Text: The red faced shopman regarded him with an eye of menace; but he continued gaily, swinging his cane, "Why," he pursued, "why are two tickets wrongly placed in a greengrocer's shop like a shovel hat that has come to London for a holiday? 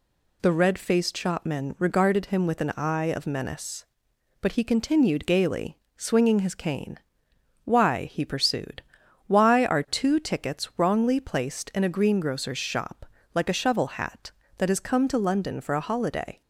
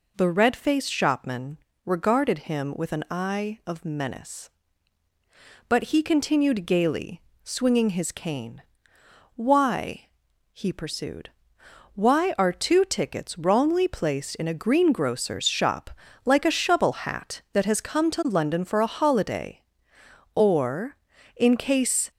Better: first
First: pauses between "shop" and "like"; slight; at 13.0 s; 0.28 s long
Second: pauses between "shopman" and "regarded"; slight; at 1.5 s; 0.26 s long // pauses between "shop" and "like"; slight; at 15.9 s; 0.34 s long // goes on to say "Or in case"; strong; from 20.3 s on; 1.7 s long

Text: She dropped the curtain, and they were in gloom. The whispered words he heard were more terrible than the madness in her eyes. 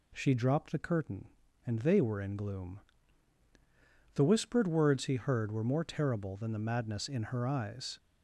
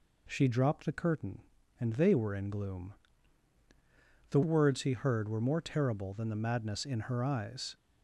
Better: first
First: none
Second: skips "whispered"; at 4.4 s

